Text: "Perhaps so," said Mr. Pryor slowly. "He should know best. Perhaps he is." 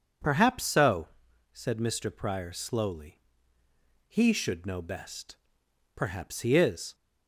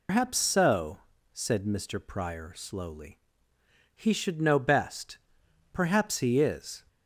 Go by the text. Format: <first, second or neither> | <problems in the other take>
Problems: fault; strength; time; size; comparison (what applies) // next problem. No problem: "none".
first | loses the start of "Perhaps"; at 0.0 s; 145 ms